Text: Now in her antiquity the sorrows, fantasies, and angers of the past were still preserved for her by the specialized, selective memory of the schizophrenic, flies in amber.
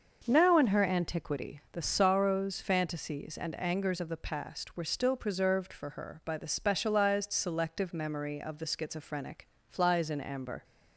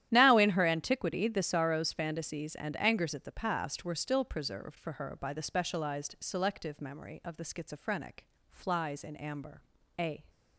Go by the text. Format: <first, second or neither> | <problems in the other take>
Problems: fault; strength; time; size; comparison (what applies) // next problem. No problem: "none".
first | starts louder than the rest; strong; until 1.1 s; 12 dB; also in the first // goes on to say "A"; slight; from 9.9 s on; 0.28 s long